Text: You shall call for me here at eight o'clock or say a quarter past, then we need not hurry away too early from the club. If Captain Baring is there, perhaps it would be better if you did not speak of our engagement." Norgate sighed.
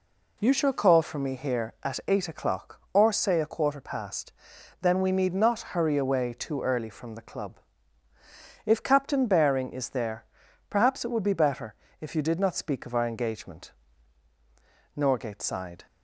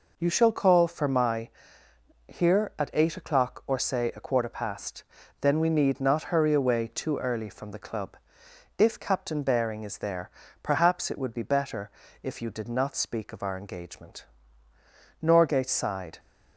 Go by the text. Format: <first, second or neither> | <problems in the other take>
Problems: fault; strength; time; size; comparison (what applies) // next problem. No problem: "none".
first | says "my" for "me"; at 1.0 s // pauses between "better" and "if"; slight; at 11.9 s; 0.32 s long; slight in the first